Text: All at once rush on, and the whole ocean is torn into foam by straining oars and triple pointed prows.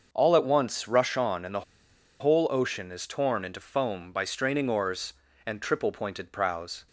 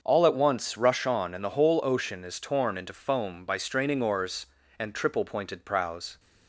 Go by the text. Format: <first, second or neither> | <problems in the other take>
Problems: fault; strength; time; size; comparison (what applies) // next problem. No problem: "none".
second | starts louder than the rest; until 1.1 s; 6.5 dB; also in the second // pauses between "the" and "whole"; noticeable; at 1.6 s; 0.58 s long